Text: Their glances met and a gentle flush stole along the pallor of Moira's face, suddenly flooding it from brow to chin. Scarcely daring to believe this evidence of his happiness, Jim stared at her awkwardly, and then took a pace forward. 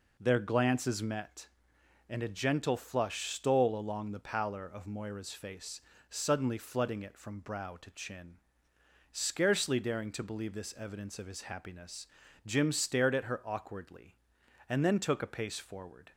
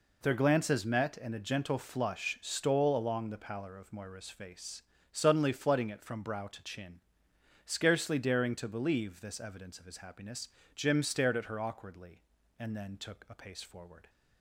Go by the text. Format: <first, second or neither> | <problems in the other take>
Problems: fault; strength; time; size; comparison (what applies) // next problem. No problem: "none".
neither | none